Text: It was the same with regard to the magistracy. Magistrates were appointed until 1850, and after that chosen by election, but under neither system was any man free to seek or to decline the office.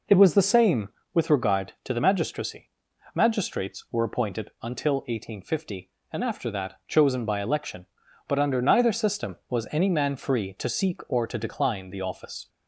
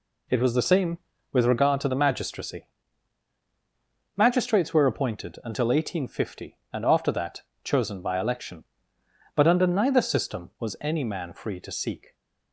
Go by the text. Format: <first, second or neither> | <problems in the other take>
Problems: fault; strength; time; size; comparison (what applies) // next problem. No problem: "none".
first | pauses between "that" and "chosen"; slight; at 7.4 s; 0.22 s long // stops before "or to decline the office"; at 12.1 s